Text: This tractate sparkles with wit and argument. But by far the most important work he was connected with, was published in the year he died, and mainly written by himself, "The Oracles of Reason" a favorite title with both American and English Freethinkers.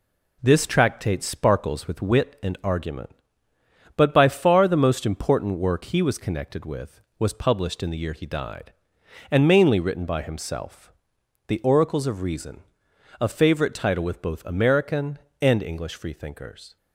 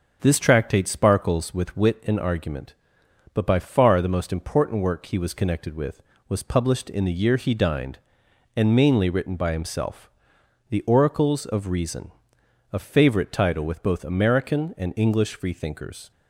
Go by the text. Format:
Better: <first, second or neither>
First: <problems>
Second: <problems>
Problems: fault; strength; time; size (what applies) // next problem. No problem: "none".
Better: first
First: pauses between "Reason" and "a"; noticeable; at 12.6 s; 0.60 s long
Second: says "dined" for "died"; at 7.5 s // pauses between "Reason" and "a"; noticeable; at 12.1 s; 0.60 s long